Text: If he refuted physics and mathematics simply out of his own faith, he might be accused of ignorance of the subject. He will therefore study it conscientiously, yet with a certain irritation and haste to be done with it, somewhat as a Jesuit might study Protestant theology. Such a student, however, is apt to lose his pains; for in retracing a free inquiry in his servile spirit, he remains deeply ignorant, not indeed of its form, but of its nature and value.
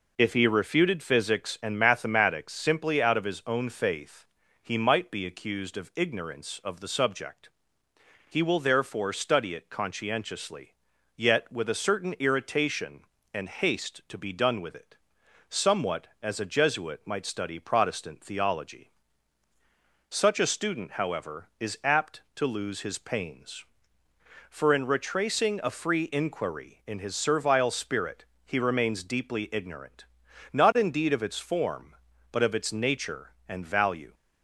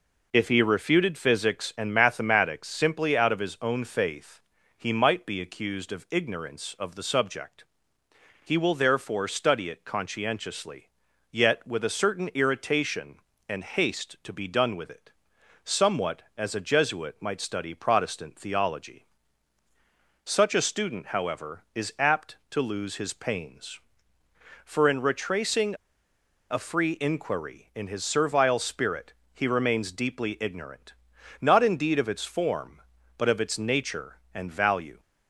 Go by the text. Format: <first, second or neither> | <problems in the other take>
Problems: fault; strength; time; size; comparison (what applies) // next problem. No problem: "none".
first | pauses between "retracing" and "a"; noticeable; at 25.7 s; 0.76 s long